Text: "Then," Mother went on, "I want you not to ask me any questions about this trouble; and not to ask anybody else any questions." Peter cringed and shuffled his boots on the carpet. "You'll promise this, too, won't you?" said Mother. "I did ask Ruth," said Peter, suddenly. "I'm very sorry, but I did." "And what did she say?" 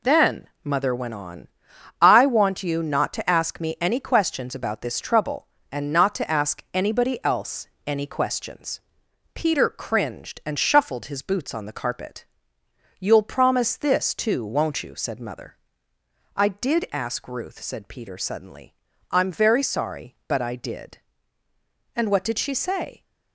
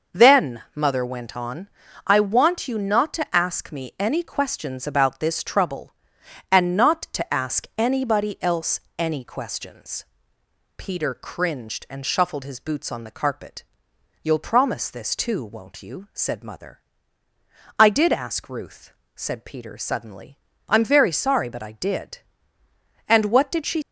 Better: first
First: pauses between "else" and "any"; slight; at 7.6 s; 0.20 s long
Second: pauses between "else" and "any"; slight; at 8.8 s; 0.16 s long // stops before "say"; at 23.8 s

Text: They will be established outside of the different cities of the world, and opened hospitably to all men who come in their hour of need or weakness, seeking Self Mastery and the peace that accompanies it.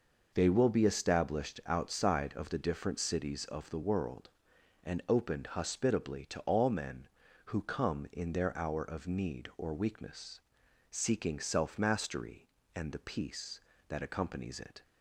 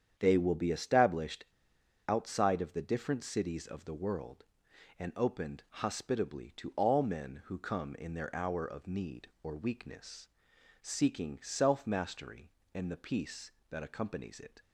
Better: first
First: none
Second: starts louder than the rest; strong; until 1.1 s; 8 dB // pauses between "established" and "outside"; noticeable; at 1.4 s; 0.63 s long

